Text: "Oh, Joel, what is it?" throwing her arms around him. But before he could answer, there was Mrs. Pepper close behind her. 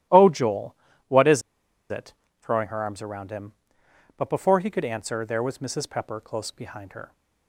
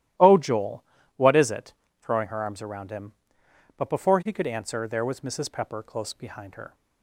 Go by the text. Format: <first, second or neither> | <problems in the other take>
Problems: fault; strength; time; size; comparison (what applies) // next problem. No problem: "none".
second | starts louder than the rest; strong; until 1.9 s; 13.5 dB; strong in the second // pauses between "is" and "it"; noticeable; at 1.4 s; 0.48 s long